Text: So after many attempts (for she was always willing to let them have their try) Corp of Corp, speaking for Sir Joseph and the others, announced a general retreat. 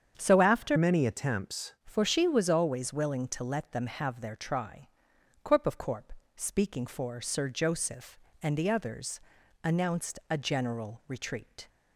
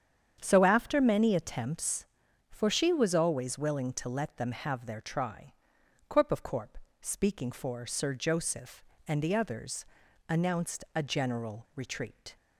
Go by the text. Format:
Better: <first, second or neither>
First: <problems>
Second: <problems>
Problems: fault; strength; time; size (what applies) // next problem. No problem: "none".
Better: second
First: starts louder than the rest; strong; until 1.1 s; 8 dB // changes voice from "many" to "attempts"; from 0.7 to 1.7 s; 1.0 s long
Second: starts louder than the rest; strong; until 1.4 s; 8.5 dB